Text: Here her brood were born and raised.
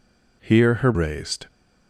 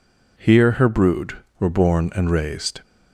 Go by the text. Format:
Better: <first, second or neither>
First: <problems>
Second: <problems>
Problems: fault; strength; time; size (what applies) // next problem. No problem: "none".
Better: second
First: skips "brood were born and"; at 0.9 s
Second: none